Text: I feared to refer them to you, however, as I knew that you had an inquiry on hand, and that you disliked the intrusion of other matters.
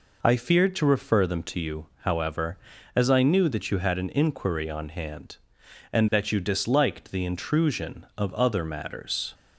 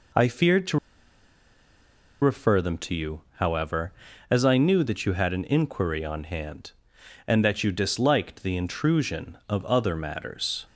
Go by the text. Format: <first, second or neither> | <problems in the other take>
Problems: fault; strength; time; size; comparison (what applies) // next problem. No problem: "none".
first | pauses between "to" and "refer"; strong; at 0.7 s; 1.4 s long